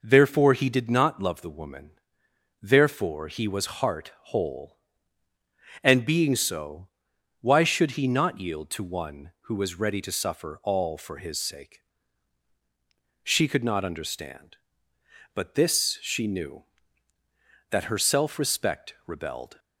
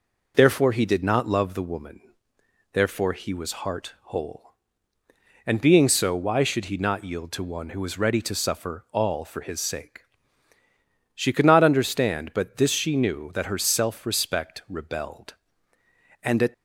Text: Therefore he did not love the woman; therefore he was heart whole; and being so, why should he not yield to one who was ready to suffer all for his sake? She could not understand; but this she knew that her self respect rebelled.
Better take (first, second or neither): first